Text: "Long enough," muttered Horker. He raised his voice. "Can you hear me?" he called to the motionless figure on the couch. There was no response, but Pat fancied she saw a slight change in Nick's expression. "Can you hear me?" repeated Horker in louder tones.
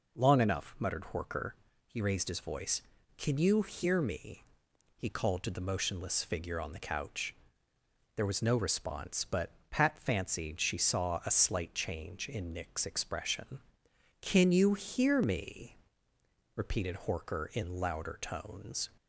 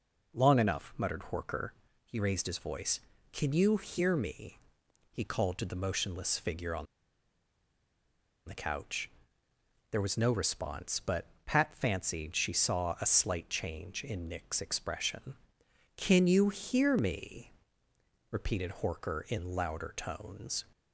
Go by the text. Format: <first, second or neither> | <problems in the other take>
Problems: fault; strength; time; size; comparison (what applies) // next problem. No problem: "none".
first | pauses between "on" and "the"; strong; at 6.8 s; 1.6 s long // pauses between "but" and "Pat"; slight; at 11.2 s; 0.20 s long; slight in the first